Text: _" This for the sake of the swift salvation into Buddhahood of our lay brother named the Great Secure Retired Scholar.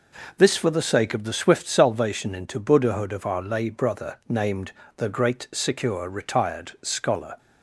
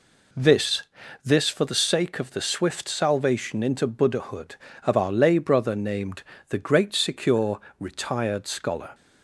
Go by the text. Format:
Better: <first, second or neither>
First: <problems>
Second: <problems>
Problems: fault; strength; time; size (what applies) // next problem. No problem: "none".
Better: first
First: pauses between "named" and "the"; slight; at 4.7 s; 0.24 s long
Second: says "This" twice; at 1.2 s // pauses between "named" and "the"; slight; at 6.2 s; 0.28 s long // pauses between "Secure" and "Retired"; slight; at 7.5 s; 0.20 s long